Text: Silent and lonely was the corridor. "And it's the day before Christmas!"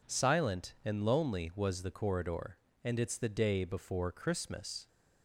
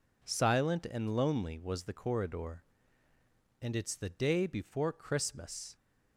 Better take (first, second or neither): neither